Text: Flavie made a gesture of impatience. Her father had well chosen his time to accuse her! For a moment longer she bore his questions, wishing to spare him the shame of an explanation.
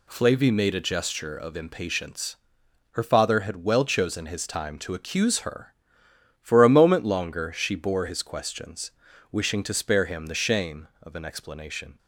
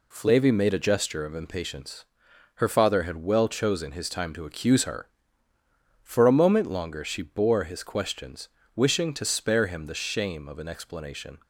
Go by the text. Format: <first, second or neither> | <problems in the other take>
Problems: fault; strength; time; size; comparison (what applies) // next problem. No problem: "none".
neither | none